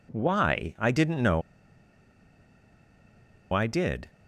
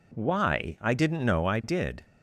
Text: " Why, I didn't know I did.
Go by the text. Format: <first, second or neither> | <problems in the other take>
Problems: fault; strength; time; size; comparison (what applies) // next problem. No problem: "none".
second | pauses between "know" and "I"; strong; at 1.4 s; 2.1 s long